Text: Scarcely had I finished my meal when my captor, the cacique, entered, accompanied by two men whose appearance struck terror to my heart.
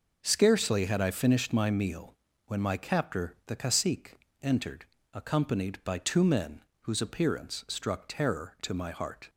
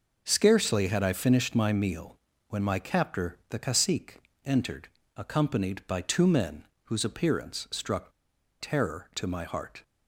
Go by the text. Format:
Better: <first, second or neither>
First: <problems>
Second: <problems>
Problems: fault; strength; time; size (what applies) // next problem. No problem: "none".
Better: first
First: pauses between "meal" and "when"; slight; at 2.1 s; 0.32 s long // pauses between "men" and "whose"; slight; at 6.6 s; 0.20 s long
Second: pauses between "meal" and "when"; slight; at 2.1 s; 0.32 s long // pauses between "men" and "whose"; slight; at 6.6 s; 0.20 s long // pauses between "struck" and "terror"; noticeable; at 8.0 s; 0.51 s long